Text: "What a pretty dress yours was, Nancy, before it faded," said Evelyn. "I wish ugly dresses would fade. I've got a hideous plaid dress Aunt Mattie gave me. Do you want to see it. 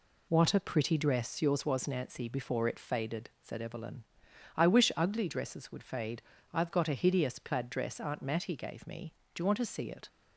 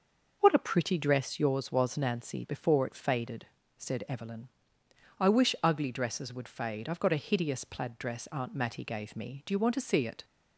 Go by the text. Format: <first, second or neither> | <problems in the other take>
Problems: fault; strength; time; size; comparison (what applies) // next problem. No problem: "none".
neither | none